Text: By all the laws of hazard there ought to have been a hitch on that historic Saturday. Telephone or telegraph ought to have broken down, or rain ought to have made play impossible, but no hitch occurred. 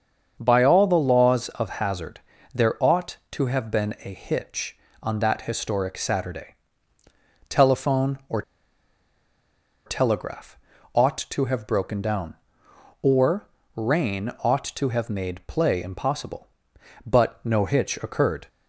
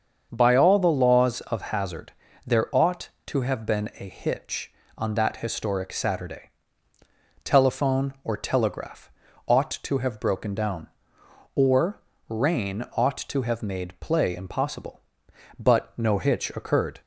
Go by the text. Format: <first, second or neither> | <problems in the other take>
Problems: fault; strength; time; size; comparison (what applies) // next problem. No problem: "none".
second | starts louder than the rest; until 1.4 s; 7 dB; also in the second // pauses between "hazard" and "there"; slight; at 2.1 s; 0.34 s long; slight in the second // pauses between "or" and "telegraph"; strong; at 8.4 s; 1.4 s long // pauses between "telegraph" and "ought"; slight; at 10.5 s; 0.36 s long; slight in the second // pauses between "or" and "rain"; slight; at 13.4 s; 0.28 s long; slight in the second